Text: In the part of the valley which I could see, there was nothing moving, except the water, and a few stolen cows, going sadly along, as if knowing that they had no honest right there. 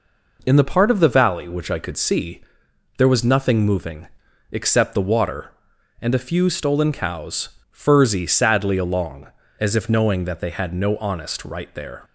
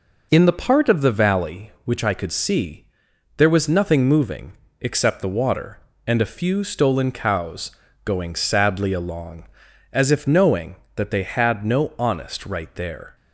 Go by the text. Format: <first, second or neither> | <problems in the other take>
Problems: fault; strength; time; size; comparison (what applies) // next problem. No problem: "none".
second | says "furzy" for "going"; at 7.7 s